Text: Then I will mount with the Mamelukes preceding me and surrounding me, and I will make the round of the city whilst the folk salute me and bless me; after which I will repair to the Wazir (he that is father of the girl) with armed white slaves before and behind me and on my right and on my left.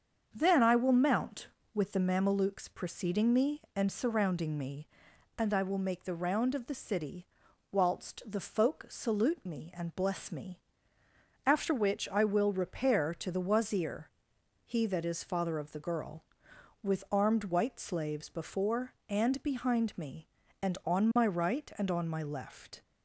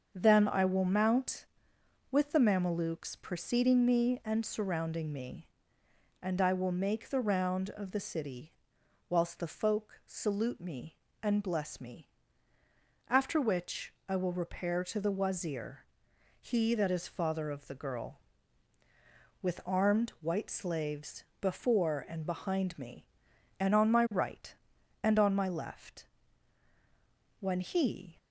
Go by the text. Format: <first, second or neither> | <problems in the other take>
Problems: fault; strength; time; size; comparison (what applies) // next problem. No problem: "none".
first | starts louder than the rest; until 1.1 s; 6.5 dB; strong in the first // pauses between "city" and "whilst"; noticeable; at 8.5 s; 0.56 s long; also in the first // pauses between "slaves" and "before"; slight; at 21.2 s; 0.16 s long // goes on to say "When he"; noticeable; from 27.4 s on; 0.76 s long